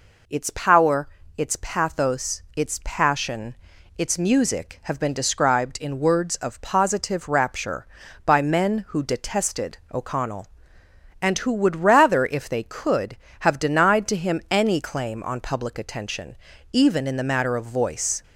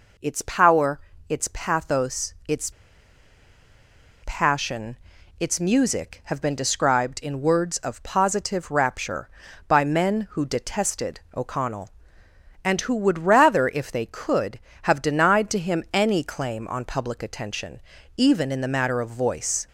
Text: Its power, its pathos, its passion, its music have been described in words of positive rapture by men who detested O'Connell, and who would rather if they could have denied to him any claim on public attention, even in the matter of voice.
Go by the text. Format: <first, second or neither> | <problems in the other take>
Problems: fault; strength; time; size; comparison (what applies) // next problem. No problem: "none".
first | pauses between "its" and "passion"; strong; at 2.7 s; 1.5 s long // pauses between "detested" and "O'Connell"; slight; at 11.1 s; 0.16 s long; slight in the first